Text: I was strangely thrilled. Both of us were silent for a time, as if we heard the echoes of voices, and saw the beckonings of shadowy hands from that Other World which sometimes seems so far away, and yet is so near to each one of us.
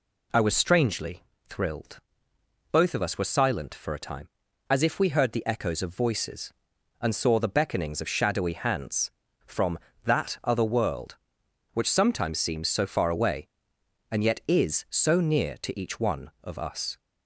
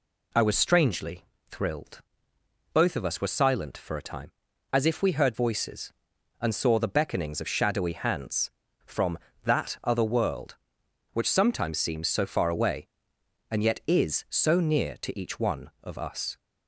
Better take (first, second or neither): first